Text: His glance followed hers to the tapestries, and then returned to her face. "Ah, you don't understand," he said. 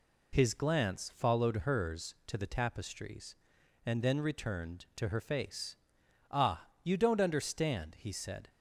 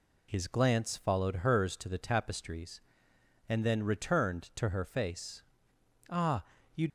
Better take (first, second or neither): first